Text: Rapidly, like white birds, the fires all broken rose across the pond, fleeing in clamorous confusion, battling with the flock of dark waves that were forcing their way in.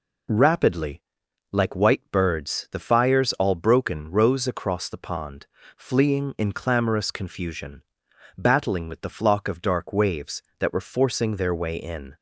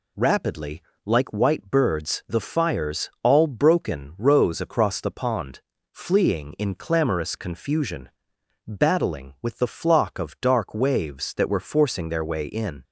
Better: neither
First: none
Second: none

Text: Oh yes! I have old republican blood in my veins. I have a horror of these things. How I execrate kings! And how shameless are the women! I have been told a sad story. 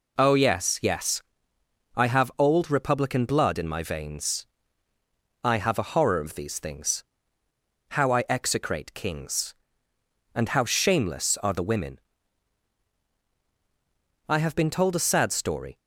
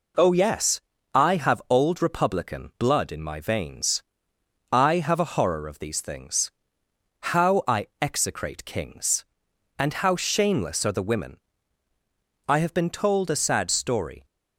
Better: second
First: says "yes" twice; at 0.8 s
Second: none

